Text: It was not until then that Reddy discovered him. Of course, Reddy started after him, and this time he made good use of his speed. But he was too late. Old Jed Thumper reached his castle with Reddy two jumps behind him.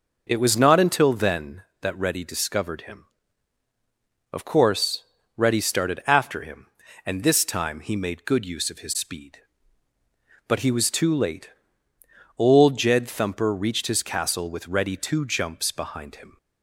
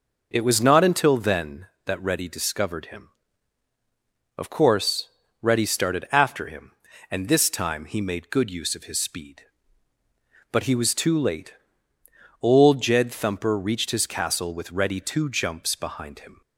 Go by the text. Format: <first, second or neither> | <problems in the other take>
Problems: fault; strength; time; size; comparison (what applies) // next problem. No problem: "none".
neither | none